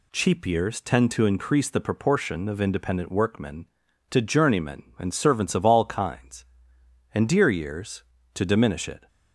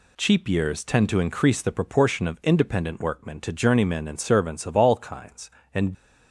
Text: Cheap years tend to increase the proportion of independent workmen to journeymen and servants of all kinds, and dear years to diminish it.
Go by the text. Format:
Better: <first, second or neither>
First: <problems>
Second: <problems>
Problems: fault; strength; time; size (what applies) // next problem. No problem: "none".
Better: first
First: none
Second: stops before "dear years to diminish it"; at 5.9 s